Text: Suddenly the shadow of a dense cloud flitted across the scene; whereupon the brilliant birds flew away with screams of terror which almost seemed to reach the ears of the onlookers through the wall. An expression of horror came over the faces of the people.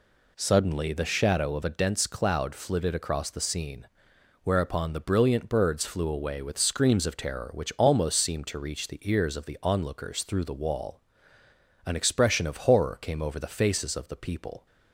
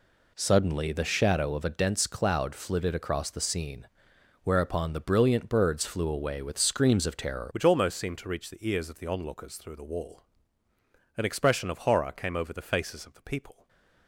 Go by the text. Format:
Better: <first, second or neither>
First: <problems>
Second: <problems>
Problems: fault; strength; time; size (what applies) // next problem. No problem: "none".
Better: first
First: none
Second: changes voice at "which"; from 7.5 s on; 6.1 s long // stays silent after the last word; slight; from 13.5 s on; 0.5 s long